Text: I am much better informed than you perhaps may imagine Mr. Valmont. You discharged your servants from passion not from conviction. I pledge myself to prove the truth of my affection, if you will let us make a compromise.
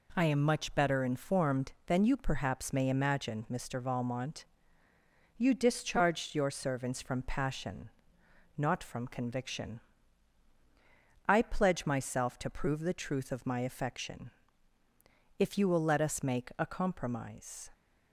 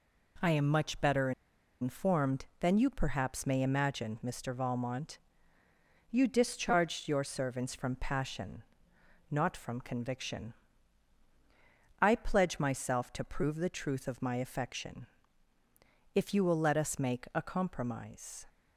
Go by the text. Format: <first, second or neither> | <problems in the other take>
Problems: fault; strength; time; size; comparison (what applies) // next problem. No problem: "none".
first | pauses between "better" and "informed"; noticeable; at 1.3 s; 0.50 s long // pauses between "passion" and "not"; noticeable; at 8.6 s; 0.68 s long; noticeable in the first